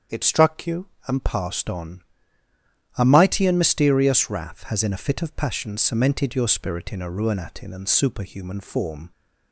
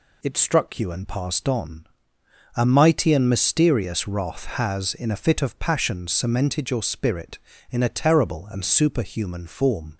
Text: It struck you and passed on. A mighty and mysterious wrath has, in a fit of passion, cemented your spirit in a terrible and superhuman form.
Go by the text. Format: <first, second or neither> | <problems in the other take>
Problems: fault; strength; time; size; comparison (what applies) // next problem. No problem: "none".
second | starts louder than the rest; strong; until 1.3 s; 7 dB // says "ruinatin" for "terrible"; at 7.0 s